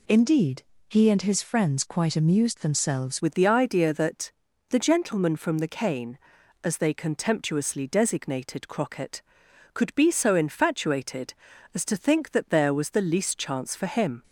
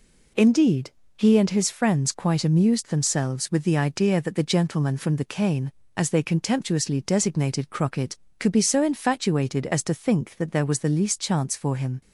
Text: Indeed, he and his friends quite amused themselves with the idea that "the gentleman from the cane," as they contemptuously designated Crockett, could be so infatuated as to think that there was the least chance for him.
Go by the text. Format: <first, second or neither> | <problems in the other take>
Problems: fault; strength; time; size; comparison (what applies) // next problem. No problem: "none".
second | changes voice at "with"; from 3.2 s on; 11.0 s long // pauses between "that" and "the"; at 4.3 s; 0.40 s long